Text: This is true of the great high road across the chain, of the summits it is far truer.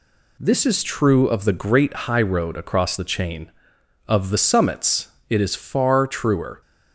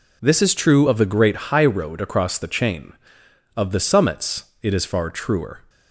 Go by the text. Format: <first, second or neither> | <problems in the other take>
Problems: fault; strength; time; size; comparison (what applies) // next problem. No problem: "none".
neither | pauses between "summits" and "it"; slight; the same in both